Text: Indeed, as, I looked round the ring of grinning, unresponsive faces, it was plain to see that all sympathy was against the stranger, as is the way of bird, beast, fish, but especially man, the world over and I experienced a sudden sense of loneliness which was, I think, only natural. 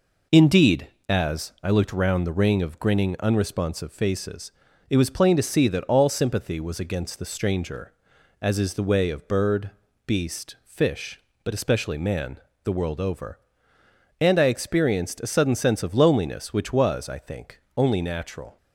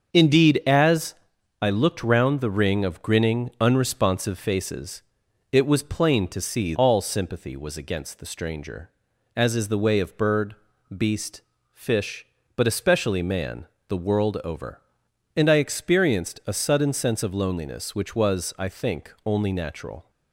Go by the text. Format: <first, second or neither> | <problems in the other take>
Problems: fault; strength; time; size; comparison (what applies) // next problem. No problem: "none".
first | starts louder than the rest; until 1.1 s; 6.5 dB // skips "that"; at 6.7 s